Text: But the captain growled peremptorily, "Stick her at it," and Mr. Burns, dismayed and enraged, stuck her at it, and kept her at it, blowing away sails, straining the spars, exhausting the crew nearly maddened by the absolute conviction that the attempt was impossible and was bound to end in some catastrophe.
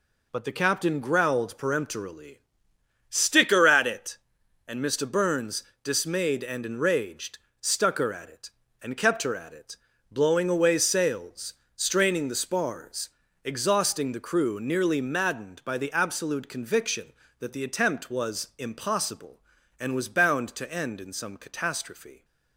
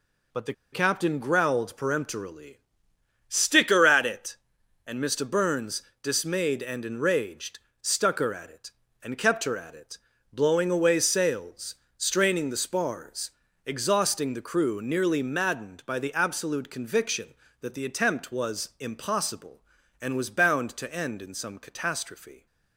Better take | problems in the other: first | pauses between "the" and "captain"; slight; at 0.5 s; 0.20 s long

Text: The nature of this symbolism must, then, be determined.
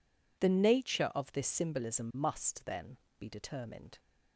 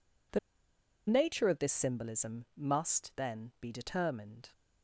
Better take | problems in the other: first | pauses between "The" and "nature"; noticeable; at 0.3 s; 0.70 s long

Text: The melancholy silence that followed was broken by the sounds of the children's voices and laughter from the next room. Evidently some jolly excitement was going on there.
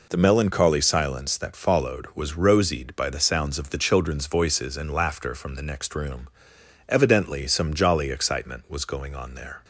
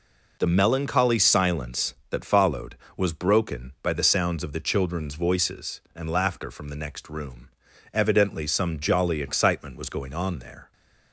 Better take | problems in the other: second | says "rosied" for "broken"; at 2.3 s

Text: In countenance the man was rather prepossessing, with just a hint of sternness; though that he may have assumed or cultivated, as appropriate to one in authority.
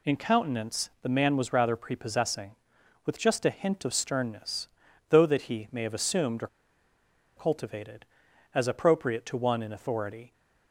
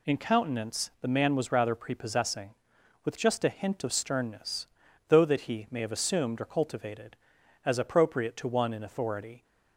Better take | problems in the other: second | pauses between "or" and "cultivated"; noticeable; at 6.4 s; 0.89 s long

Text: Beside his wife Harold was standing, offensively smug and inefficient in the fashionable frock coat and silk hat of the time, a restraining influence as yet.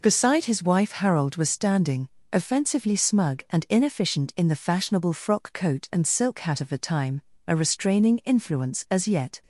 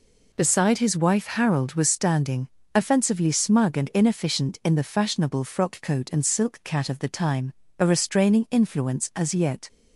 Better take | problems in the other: first | says "cat" for "hat"; at 6.6 s

